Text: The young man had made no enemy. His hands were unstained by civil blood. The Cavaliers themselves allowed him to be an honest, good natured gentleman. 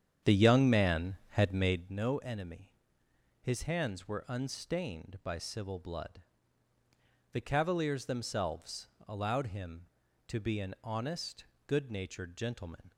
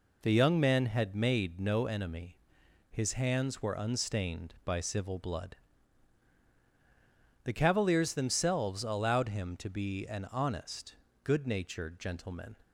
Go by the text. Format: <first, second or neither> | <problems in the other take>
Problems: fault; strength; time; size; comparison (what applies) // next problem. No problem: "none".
second | starts louder than the rest; strong; until 2.0 s; 8.5 dB // pauses between "themselves" and "allowed"; slight; at 8.8 s; 0.20 s long